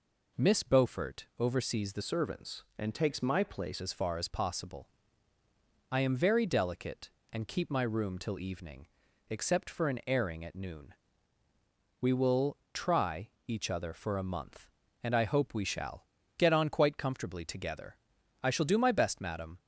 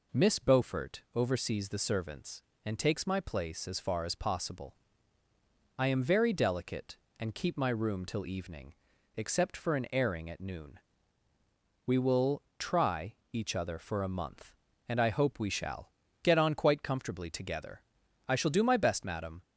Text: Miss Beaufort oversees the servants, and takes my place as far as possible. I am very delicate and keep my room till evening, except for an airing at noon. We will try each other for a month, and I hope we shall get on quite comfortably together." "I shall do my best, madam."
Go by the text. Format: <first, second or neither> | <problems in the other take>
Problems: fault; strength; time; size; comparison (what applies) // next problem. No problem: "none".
second | changes voice from "servants" to "place"; from 2.0 to 3.8 s; 1.8 s long // pauses between "will" and "try"; slight; at 12.5 s; 0.16 s long; slight in the second // pauses between "try" and "each"; slight; at 13.3 s; 0.18 s long; slight in the second // pauses between "shall" and "get"; slight; at 16.0 s; 0.34 s long; slight in the second